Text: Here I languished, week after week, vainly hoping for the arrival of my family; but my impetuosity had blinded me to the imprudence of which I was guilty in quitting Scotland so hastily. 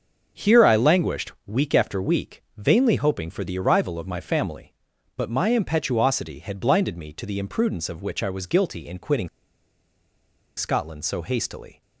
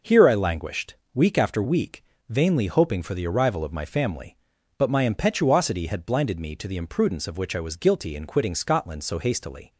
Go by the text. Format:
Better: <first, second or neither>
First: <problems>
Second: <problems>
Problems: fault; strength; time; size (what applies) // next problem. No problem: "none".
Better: second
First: starts louder than the rest; until 1.5 s; 6.5 dB // pauses between "quitting" and "Scotland"; strong; at 9.2 s; 1.3 s long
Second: none